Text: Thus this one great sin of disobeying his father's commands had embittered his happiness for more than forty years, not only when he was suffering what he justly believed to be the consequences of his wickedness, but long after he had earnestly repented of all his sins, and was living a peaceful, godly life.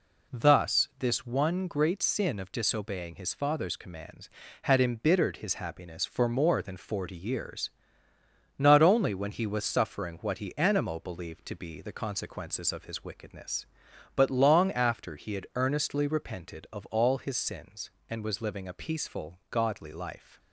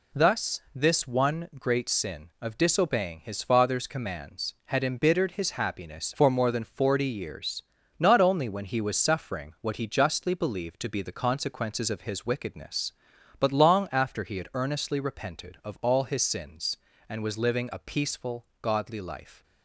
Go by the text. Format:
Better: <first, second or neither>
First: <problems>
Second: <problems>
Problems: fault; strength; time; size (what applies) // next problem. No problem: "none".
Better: second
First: says "animo" for "justly"; at 10.5 s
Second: none